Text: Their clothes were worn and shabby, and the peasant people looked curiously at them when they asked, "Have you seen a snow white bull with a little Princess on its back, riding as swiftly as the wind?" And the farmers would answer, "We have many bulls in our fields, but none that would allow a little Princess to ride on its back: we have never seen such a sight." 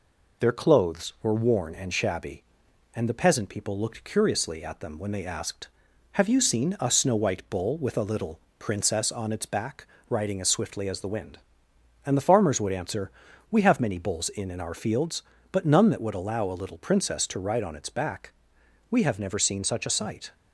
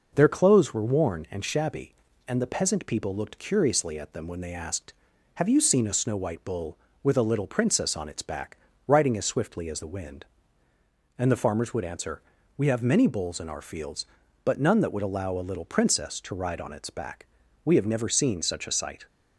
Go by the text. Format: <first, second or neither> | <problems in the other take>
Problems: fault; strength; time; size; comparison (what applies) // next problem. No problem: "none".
second | pauses between "little" and "Princess"; slight; at 8.3 s; 0.20 s long // says "in" twice; at 14.5 s